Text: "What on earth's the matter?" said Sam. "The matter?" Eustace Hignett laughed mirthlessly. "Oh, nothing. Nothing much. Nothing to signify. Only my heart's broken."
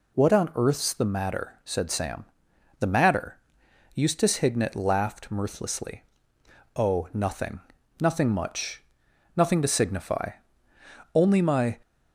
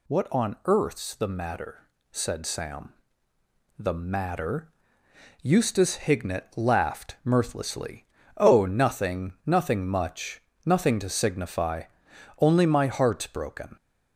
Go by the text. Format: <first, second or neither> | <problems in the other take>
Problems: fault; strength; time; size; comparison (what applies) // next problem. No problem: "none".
second | stops before "heart's broken"; at 11.8 s